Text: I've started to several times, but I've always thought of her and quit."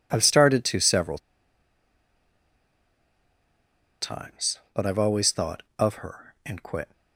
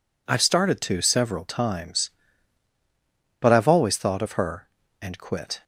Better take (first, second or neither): second